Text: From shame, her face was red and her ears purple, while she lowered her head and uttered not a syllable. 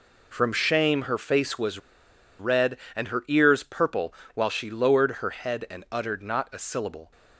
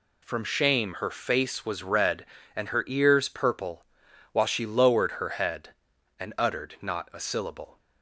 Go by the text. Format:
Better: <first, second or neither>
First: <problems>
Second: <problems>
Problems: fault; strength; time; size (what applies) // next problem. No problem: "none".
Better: second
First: pauses between "was" and "red"; noticeable; at 1.7 s; 0.61 s long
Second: none